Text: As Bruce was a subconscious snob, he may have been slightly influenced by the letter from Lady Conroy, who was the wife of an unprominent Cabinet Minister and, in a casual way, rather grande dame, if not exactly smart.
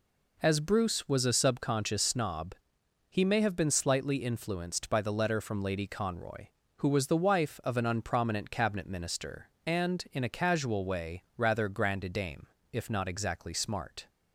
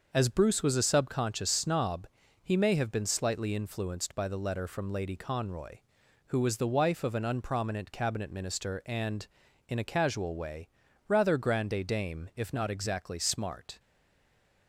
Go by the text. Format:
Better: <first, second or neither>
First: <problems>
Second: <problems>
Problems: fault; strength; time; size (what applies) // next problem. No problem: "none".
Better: first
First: none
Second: starts louder than the rest; noticeable; until 1.1 s; 6 dB // stays silent after the last word; slight; from 13.7 s on; 0.9 s long